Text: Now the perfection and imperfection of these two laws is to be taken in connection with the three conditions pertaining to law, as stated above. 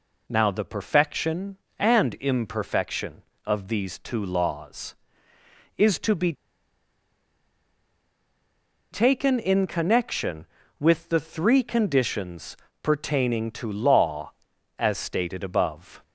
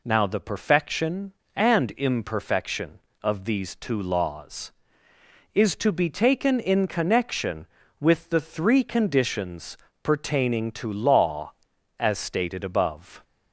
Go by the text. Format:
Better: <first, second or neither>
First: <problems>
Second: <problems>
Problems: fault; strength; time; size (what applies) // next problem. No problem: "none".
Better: second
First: pauses between "be" and "taken"; strong; at 6.3 s; 2.5 s long // pauses between "conditions" and "pertaining"; slight; at 12.5 s; 0.24 s long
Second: pauses between "conditions" and "pertaining"; slight; at 9.7 s; 0.24 s long